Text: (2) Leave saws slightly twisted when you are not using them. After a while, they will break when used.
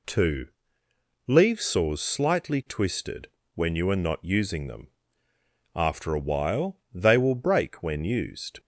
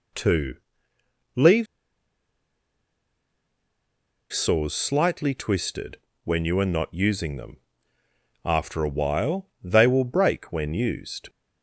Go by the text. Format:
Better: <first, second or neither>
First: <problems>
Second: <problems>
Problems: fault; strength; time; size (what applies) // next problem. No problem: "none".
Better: first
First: pauses between "twisted" and "when"; slight; at 3.2 s; 0.26 s long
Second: pauses between "Leave" and "saws"; strong; at 1.6 s; 2.6 s long // pauses between "twisted" and "when"; slight; at 5.9 s; 0.26 s long